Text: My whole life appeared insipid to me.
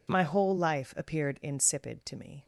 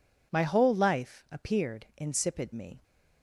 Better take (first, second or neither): first